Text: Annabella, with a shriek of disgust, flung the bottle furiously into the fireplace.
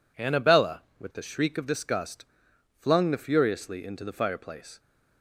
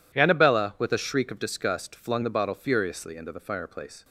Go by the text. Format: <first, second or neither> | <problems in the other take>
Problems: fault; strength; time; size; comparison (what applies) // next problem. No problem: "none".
second | skips "bottle"; at 3.1 s